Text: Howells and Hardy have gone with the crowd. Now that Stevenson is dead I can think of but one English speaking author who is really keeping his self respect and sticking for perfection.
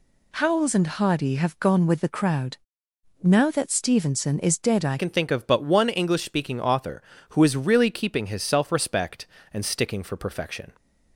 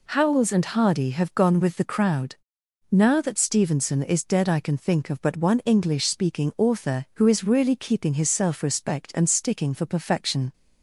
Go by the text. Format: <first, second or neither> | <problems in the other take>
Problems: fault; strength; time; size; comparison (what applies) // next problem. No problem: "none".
second | changes voice at "can"; from 4.9 s on; 5.8 s long